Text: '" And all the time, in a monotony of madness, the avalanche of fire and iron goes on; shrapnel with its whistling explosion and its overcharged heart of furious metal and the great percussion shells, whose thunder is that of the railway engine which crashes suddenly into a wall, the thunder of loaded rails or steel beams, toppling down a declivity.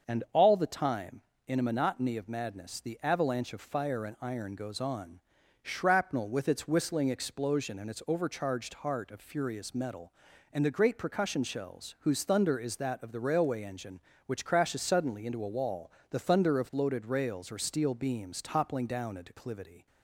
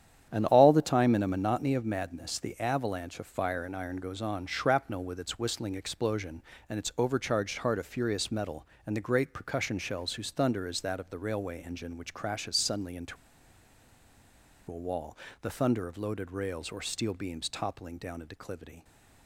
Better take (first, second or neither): first